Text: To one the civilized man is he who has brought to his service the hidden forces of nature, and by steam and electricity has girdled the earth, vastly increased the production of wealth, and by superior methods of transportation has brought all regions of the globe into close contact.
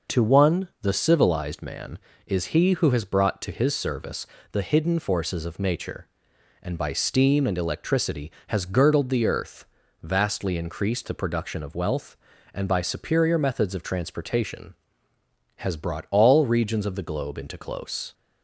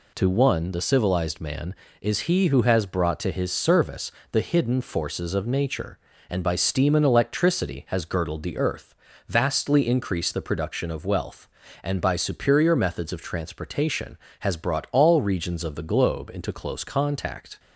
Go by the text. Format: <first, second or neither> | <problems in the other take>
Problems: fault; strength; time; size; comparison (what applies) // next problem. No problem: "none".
second | pauses between "service" and "the"; slight; at 4.2 s; 0.26 s long; slight in the second // stops before "contact"; at 18.1 s